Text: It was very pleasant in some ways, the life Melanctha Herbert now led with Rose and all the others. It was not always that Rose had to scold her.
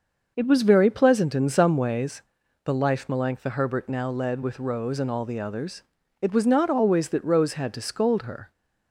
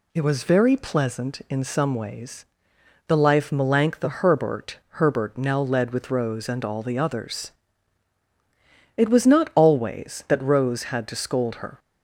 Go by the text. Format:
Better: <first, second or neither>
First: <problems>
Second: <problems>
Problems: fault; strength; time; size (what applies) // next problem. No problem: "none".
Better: first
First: none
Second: says "Herbert" twice; at 4.9 s